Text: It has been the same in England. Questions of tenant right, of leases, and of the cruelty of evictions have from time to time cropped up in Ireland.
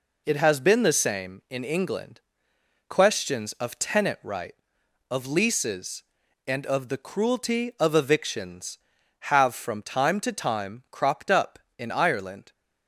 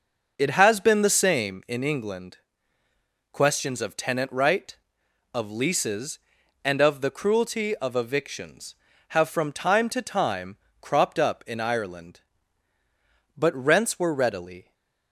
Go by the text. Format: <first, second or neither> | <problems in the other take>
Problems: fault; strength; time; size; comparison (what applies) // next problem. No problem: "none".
first | pauses between "time" and "cropped"; slight; at 10.5 s; 0.24 s long // goes on to say "But rents were readily"; from 13.3 s on; 1.3 s long // stays silent after the last word; slight; from 14.6 s on; 0.5 s long